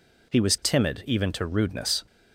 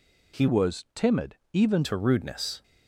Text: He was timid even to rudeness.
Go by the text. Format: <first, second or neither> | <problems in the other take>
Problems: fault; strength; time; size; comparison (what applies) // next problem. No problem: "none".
first | changes voice from "was" to "even"; from 0.4 to 1.8 s; 1.4 s long // pauses between "timid" and "even"; slight; at 1.3 s; 0.16 s long